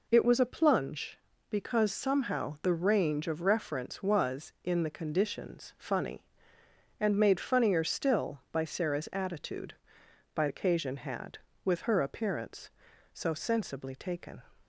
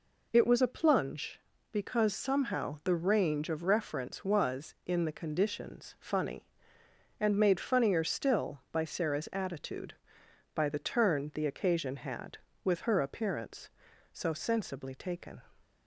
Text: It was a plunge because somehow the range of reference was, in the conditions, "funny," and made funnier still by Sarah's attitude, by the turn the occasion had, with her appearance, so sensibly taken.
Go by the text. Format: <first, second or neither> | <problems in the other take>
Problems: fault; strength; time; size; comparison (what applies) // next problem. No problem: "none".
second | skips "the turn the"; at 10.4 s